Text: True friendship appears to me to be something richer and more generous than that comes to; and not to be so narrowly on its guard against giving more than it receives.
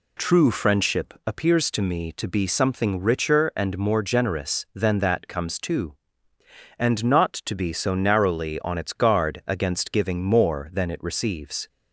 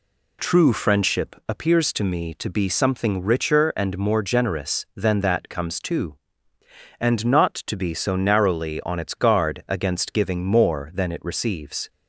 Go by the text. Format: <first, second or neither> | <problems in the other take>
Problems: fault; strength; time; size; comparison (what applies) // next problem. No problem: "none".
neither | none